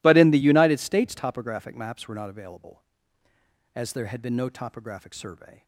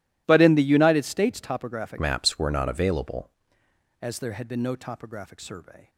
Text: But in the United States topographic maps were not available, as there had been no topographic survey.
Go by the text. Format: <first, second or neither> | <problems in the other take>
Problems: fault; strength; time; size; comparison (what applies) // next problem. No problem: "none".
first | changes voice from "maps" to "available"; from 1.9 to 3.2 s; 1.3 s long